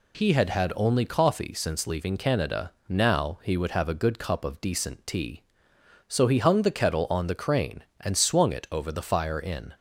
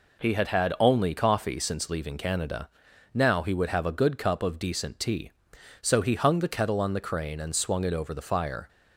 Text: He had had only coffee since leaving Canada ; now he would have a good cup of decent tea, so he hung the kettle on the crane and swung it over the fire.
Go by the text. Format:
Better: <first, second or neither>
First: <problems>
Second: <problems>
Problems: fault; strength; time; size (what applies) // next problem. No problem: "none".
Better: second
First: goes on to say "In"; slight; from 9.3 s on; 0.36 s long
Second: none